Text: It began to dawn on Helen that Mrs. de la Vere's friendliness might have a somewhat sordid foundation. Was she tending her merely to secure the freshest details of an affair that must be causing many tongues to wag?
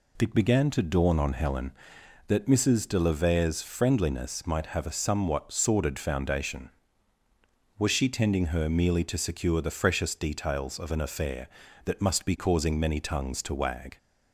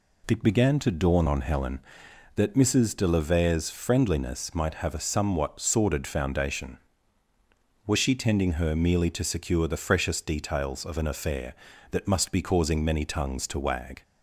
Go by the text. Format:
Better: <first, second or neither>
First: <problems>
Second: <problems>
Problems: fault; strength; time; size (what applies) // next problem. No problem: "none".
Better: neither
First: none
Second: none